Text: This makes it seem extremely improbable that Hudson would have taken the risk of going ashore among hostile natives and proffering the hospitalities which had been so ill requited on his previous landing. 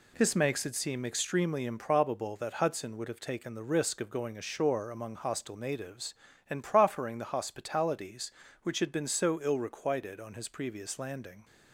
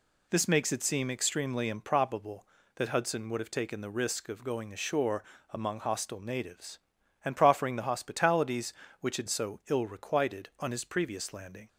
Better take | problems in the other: first | pauses between "ashore" and "among"; slight; at 5.2 s; 0.30 s long // skips "been"; at 9.2 s

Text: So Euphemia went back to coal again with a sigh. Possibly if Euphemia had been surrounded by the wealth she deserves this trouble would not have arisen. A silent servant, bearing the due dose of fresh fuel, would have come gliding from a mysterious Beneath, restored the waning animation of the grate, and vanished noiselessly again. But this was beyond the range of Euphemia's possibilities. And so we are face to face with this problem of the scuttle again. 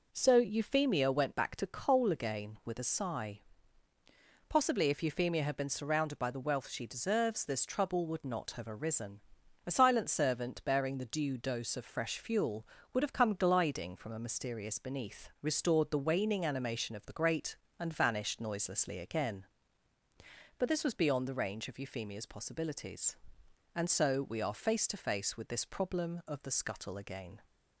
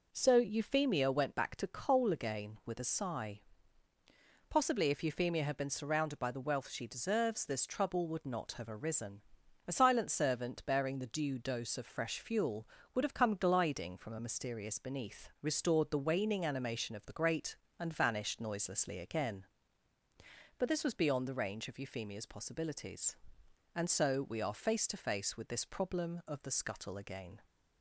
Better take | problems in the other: neither | none

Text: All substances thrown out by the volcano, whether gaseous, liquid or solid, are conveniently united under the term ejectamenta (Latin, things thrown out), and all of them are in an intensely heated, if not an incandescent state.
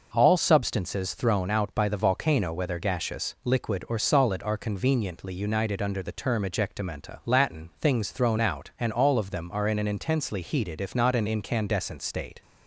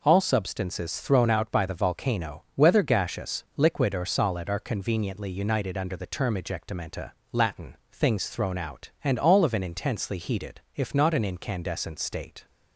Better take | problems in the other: first | skips "them are in"; at 9.5 s

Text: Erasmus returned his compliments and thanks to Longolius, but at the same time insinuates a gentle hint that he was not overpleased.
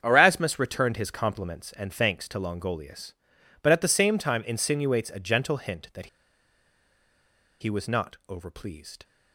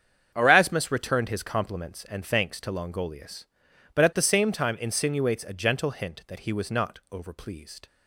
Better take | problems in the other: second | starts louder than the rest; strong; until 1.0 s; 7.5 dB; strong in the second // pauses between "that" and "he"; strong; at 6.0 s; 1.5 s long

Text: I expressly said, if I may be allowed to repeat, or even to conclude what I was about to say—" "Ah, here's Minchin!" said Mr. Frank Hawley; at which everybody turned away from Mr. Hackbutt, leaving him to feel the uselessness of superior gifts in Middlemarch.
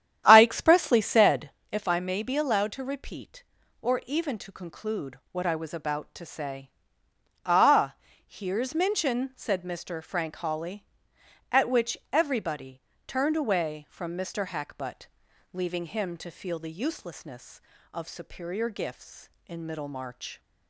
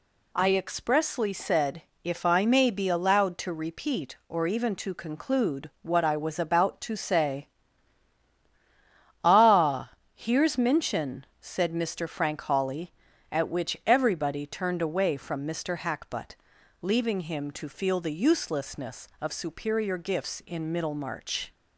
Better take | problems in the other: second | starts louder than the rest; strong; until 1.6 s; 10 dB // pauses between "conclude" and "what"; slight; at 5.1 s; 0.16 s long // pauses between "which" and "everybody"; slight; at 11.9 s; 0.16 s long // pauses between "everybody" and "turned"; slight; at 12.7 s; 0.26 s long

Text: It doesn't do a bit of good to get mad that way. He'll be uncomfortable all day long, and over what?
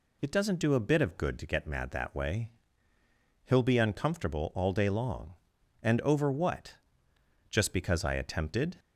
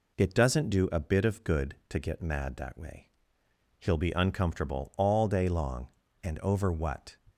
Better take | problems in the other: second | goes on to say "Just because I attempted"; noticeable; from 7.4 s on; 1.2 s long

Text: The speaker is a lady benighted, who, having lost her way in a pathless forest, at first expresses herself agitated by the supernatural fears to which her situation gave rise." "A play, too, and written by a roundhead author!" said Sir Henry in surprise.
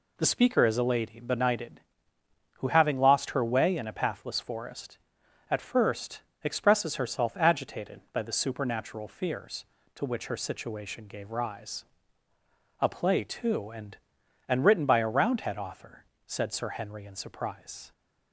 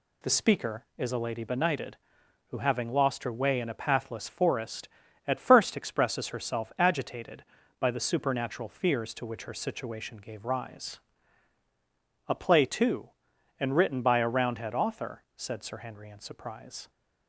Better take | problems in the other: second | pauses between "first" and "expresses"; slight; at 6.2 s; 0.22 s long // says "and" twice; at 14.4 s

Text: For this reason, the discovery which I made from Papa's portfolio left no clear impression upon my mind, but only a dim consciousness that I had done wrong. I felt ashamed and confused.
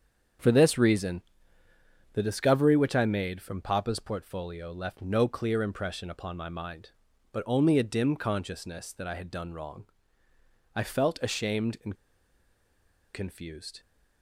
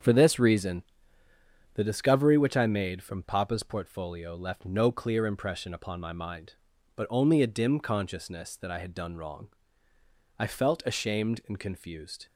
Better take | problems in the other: second | starts louder than the rest; until 2.3 s; 7 dB; also in the second // pauses between "and" and "confused"; at 11.9 s; 1.1 s long

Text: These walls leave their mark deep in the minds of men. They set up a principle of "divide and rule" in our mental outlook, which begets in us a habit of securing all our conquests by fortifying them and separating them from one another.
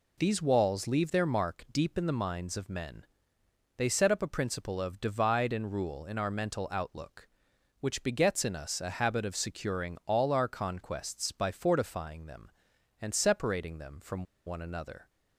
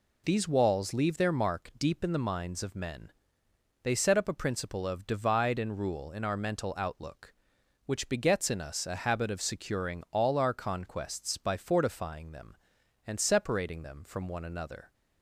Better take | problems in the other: second | pauses between "from" and "one"; slight; at 14.2 s; 0.21 s long

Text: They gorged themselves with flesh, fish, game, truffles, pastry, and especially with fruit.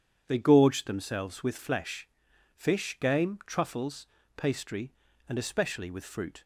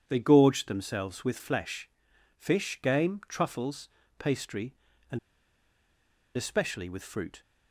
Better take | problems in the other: first | pauses between "and" and "especially"; at 5.1 s; 1.1 s long

